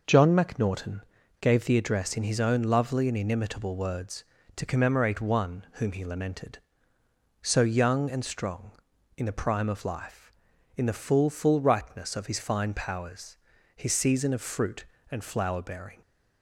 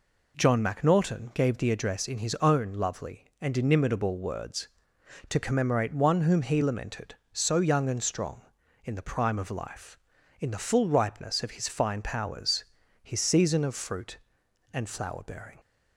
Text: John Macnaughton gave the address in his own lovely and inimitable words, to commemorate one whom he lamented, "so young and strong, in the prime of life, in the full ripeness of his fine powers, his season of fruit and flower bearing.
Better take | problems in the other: second | pauses between "Macnaughton" and "gave"; at 1.0 s; 0.40 s long // says "full" twice; at 11.2 s

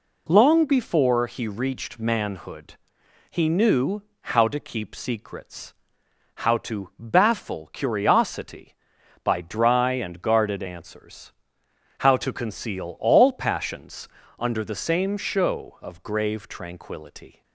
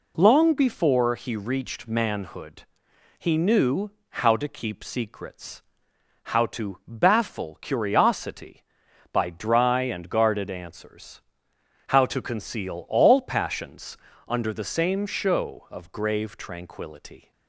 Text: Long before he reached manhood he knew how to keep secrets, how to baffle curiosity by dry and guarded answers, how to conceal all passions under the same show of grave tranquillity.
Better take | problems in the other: neither | pauses between "manhood" and "he"; noticeable; the same in both // pauses between "knew" and "how"; slight; the same in both // pauses between "passions" and "under"; slight; the same in both

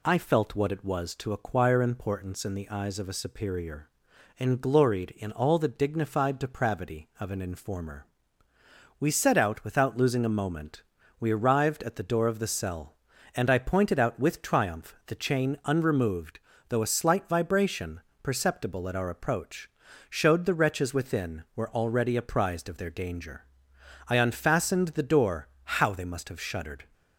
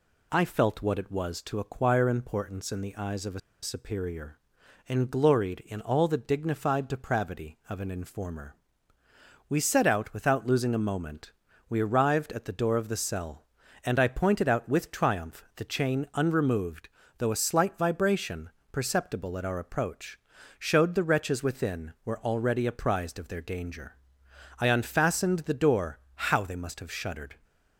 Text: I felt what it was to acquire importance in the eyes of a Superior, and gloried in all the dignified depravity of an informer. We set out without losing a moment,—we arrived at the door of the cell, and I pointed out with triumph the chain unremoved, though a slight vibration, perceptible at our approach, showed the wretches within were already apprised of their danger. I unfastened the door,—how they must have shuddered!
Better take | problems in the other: first | pauses between "a" and "Superior"; slight; at 3.3 s; 0.23 s long

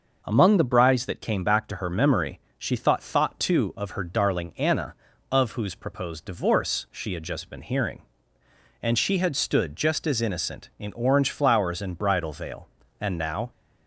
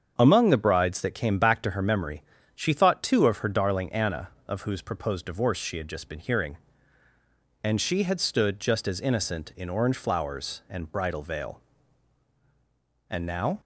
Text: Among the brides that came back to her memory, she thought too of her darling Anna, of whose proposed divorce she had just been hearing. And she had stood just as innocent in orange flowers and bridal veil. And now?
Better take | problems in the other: second | starts louder than the rest; noticeable; until 1.2 s; 6 dB; strong in the second // says "thought" twice; at 3.0 s

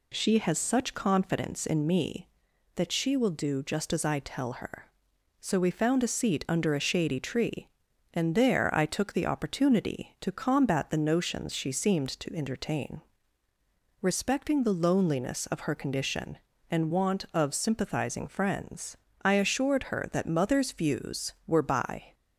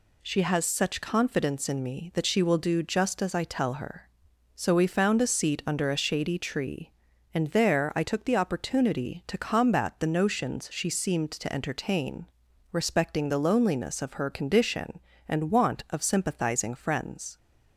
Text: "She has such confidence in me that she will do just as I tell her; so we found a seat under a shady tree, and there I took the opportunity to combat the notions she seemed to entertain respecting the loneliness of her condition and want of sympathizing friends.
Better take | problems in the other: second | pauses between "entertain" and "respecting"; at 13.0 s; 1.0 s long; noticeable in the second // goes on to say "I assured her that mother's views were by"; strong; from 19.2 s on; 2.9 s long

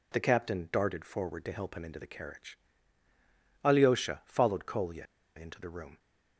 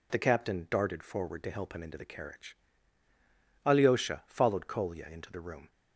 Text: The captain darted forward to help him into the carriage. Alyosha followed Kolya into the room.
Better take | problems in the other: second | pauses between "Kolya" and "into"; slight; at 5.0 s; 0.31 s long

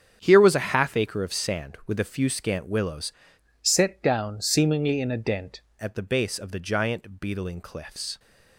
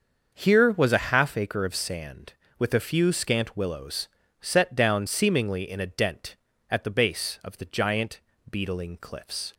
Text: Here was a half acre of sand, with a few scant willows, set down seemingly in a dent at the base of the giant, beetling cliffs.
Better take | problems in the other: second | starts louder than the rest; strong; until 1.2 s; 8 dB; also in the second // changes voice from "set" to "dent"; from 3.6 to 5.6 s; 2.0 s long

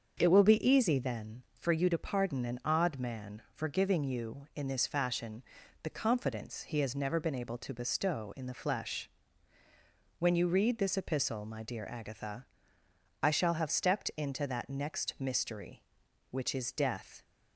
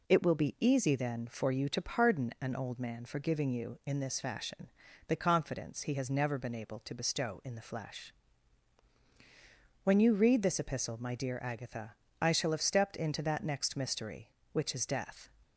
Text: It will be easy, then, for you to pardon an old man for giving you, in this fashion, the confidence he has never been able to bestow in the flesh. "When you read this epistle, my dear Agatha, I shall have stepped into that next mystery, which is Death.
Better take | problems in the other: second | starts louder than the rest; until 1.1 s; 7 dB // says "odd" for "old"; at 2.6 s

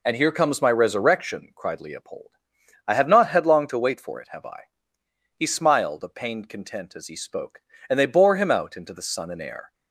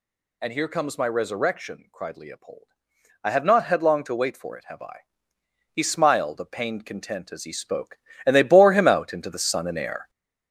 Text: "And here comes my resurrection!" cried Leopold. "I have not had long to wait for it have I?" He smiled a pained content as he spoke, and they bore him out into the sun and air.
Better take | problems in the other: first | gets louder; noticeable; throughout; 4.5 dB

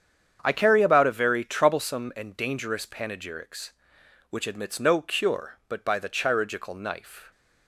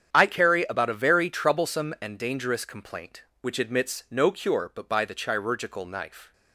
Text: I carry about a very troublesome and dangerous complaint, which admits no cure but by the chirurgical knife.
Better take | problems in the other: second | starts louder than the rest; strong; until 1.4 s; 8 dB; strong in the second // says "panegyrics" for "complaint"; at 2.8 s

